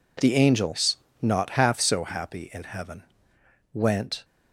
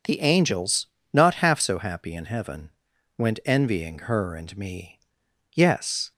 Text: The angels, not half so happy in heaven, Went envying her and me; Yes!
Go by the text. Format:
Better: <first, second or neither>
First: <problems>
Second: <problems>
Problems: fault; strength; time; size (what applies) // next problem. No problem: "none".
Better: second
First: stops before "envying her and me Yes"; at 4.2 s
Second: none